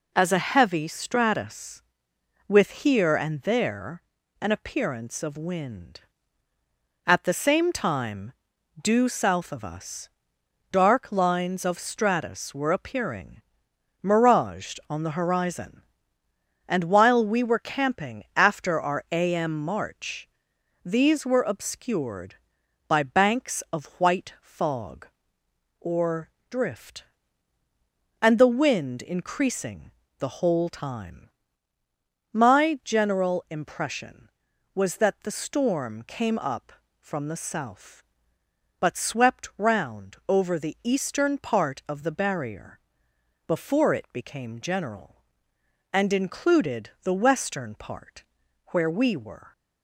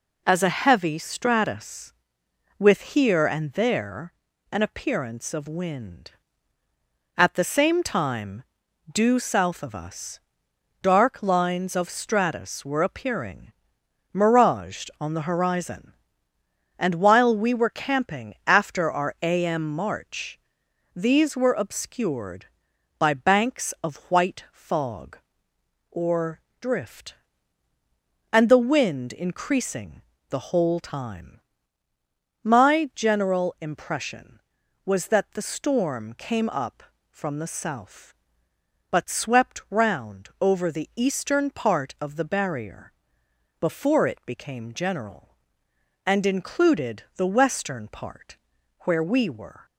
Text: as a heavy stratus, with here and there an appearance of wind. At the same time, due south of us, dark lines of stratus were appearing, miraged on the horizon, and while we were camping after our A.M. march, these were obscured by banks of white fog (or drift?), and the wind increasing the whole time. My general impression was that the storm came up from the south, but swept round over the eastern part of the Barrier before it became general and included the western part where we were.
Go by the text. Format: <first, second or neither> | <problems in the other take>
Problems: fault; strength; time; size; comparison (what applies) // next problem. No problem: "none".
neither | pauses between "there" and "an"; the same in both // pauses between "or" and "drift"; slight; the same in both // pauses between "increasing" and "the"; slight; the same in both // pauses between "Barrier" and "before"; noticeable; the same in both // pauses between "part" and "where"; the same in both